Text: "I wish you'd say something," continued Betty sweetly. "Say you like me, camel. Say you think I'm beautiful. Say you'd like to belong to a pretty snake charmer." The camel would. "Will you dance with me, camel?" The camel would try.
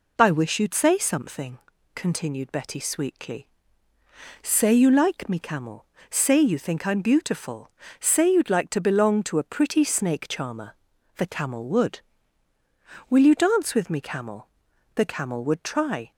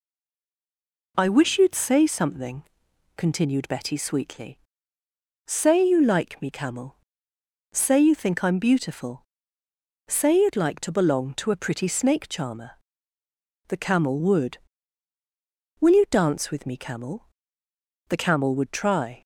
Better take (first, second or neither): first